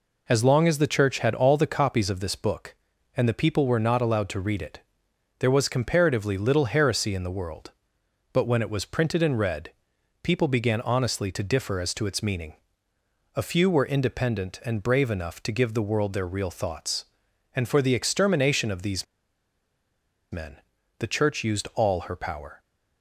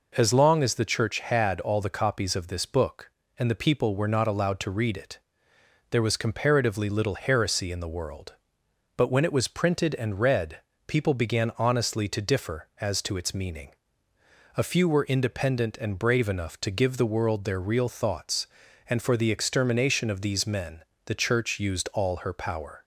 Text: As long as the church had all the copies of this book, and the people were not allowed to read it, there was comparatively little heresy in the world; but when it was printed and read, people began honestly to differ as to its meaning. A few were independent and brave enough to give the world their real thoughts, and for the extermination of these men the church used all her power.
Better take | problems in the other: second | pauses between "these" and "men"; strong; at 19.0 s; 1.2 s long // pauses between "men" and "the"; at 20.5 s; 0.42 s long; slight in the second

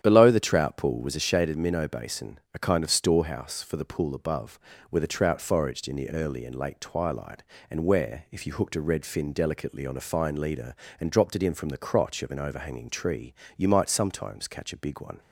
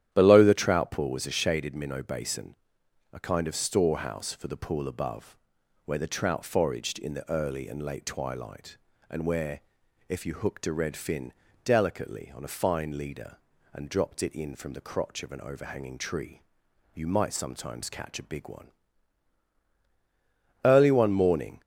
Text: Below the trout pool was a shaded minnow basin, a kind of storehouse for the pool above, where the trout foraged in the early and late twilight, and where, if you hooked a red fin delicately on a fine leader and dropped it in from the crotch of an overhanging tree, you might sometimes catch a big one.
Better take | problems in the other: first | starts louder than the rest; strong; until 1.1 s; 11 dB; strong in the first // pauses between "fin" and "delicately"; slight; at 11.3 s; 0.32 s long // goes on to say "Early one morning"; noticeable; from 20.6 s on; 0.96 s long

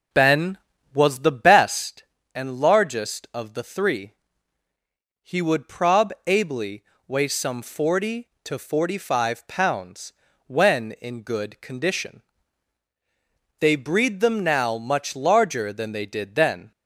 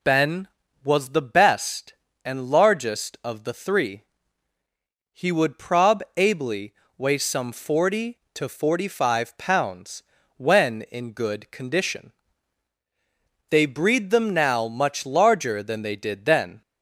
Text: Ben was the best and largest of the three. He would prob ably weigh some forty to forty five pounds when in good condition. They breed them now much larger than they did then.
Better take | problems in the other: second | starts louder than the rest; noticeable; until 2.0 s; 5.5 dB // pauses between "ably" and "weigh"; slight; at 6.8 s; 0.24 s long; slight in the second // pauses between "pounds" and "when"; slight; at 10.1 s; 0.34 s long; slight in the second

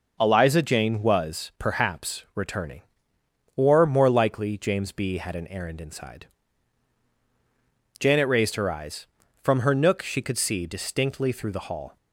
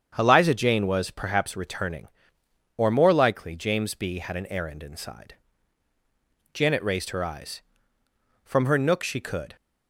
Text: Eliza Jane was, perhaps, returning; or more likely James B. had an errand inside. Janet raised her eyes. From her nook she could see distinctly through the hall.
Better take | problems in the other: first | starts louder than the rest; strong; until 1.1 s; 8 dB // stops before "see distinctly through the hall"; at 9.5 s

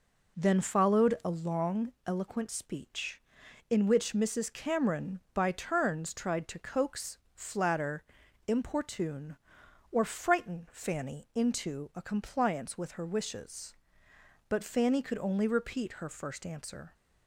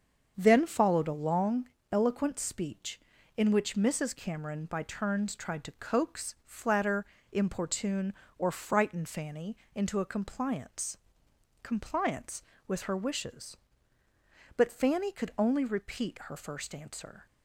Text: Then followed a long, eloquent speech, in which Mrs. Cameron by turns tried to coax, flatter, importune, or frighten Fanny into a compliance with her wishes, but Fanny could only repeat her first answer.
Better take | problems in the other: first | starts louder than the rest; until 1.3 s; 7 dB // pauses between "Fanny" and "into"; slight; at 9.5 s; 0.18 s long // says "compliance" twice; at 11.6 s

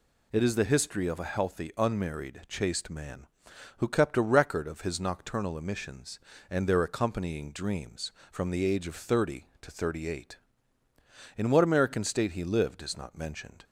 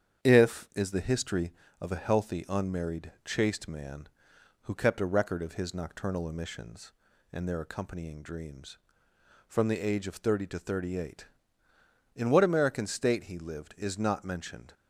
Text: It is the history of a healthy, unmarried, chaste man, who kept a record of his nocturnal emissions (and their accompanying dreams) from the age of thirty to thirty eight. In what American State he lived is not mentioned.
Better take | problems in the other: first | starts louder than the rest; strong; until 1.3 s; 8.5 dB // says "If" for "It"; at 0.2 s

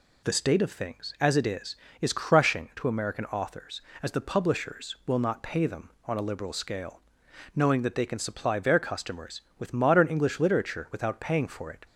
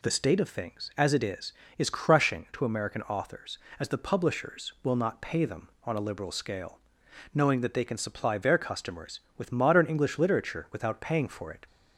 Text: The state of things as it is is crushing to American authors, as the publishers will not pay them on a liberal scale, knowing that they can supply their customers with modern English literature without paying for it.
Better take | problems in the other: neither | none

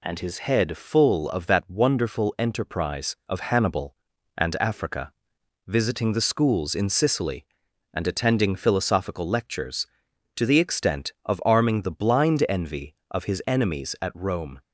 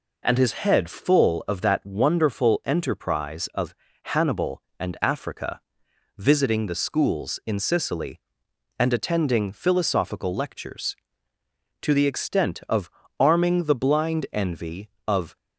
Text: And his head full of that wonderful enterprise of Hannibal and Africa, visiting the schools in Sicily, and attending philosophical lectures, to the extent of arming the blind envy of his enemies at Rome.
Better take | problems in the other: first | pauses between "of" and "Hannibal"; slight; at 3.7 s; 0.30 s long // pauses between "of" and "arming"; slight; at 12.8 s; 0.30 s long // stops before "his enemies at Rome"; at 15.3 s

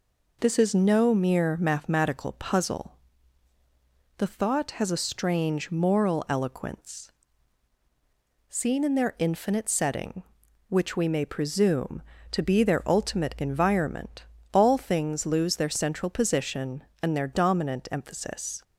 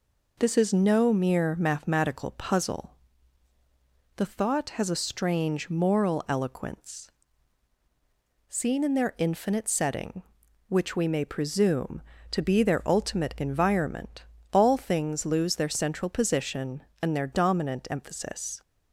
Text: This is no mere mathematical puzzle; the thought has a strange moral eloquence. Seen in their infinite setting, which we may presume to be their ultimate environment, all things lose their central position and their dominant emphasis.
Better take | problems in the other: neither | none

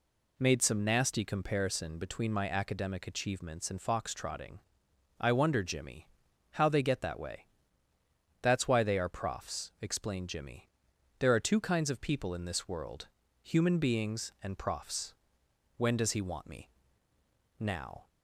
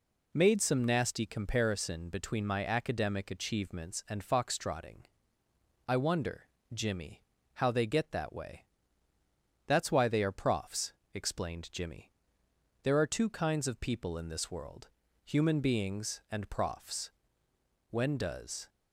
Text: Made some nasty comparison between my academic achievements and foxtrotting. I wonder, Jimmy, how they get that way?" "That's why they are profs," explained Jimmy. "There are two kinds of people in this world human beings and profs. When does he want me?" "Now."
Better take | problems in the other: first | pauses between "world" and "human"; slight; at 14.8 s; 0.36 s long; slight in the first // stops before "he want me Now"; at 18.6 s

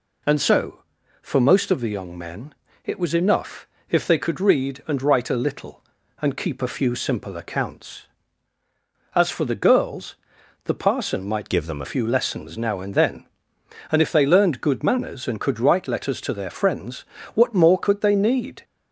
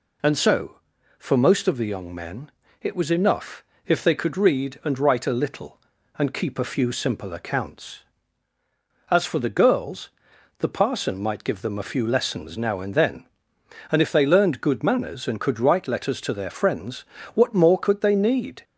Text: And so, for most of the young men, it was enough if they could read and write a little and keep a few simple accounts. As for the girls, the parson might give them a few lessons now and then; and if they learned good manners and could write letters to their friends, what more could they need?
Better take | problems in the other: second | pauses between "enough" and "if"; slight; at 3.6 s; 0.22 s long; slight in the second // changes voice from "give" to "a"; from 11.4 to 11.8 s; 0.4 s long

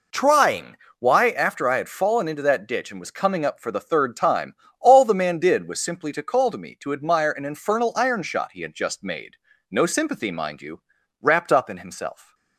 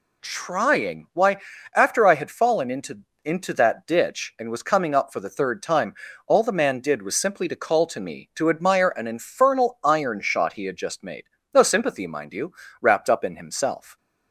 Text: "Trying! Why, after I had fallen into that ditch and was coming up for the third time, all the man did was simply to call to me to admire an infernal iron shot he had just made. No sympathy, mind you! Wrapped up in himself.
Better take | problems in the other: first | says "into" twice; at 3.2 s

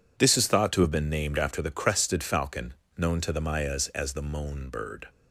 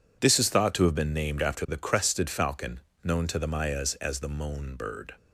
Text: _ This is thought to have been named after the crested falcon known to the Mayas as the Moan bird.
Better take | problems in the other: neither | pauses between "falcon" and "known"; slight; the same in both

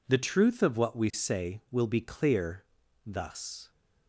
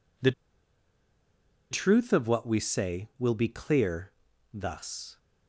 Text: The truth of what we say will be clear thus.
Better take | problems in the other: first | pauses between "The" and "truth"; strong; at 0.3 s; 1.3 s long // pauses between "clear" and "thus"; at 4.1 s; 0.40 s long; also in the first

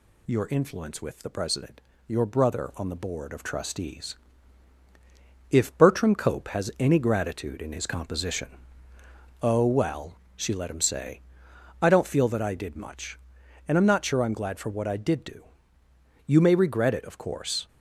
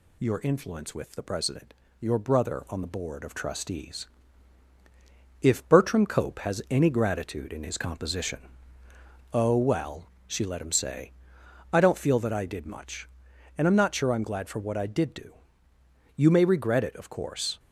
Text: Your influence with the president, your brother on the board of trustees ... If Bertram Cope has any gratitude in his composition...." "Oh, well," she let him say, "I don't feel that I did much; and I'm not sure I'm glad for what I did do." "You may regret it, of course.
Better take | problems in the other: neither | none

